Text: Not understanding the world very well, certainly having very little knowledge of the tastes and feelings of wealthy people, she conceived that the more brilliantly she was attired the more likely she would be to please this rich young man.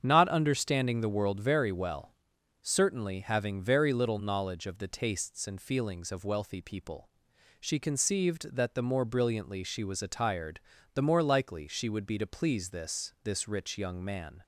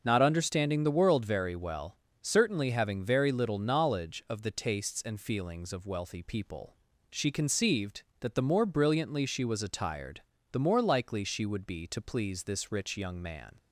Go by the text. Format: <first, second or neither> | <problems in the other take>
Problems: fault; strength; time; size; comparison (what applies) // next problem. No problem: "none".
second | starts louder than the rest; strong; until 1.0 s; 8 dB; also in the second // pauses between "attired" and "the"; slight; at 10.6 s; 0.32 s long; slight in the second // says "this" twice; at 13.2 s